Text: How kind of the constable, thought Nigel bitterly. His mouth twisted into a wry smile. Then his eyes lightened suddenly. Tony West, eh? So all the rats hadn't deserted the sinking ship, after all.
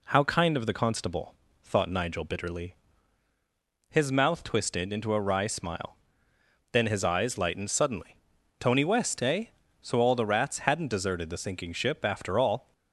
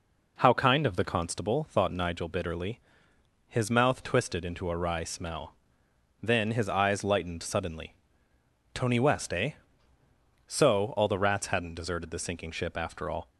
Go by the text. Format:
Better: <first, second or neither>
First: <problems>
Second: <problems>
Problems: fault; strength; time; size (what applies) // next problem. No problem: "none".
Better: first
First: none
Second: says "smell" for "smile"; at 5.0 s